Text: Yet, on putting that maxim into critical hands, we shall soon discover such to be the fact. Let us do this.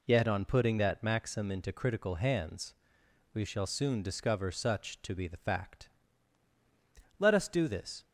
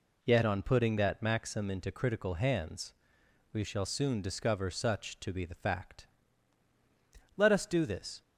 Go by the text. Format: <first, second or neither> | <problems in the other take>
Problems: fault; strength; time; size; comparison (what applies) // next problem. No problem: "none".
neither | none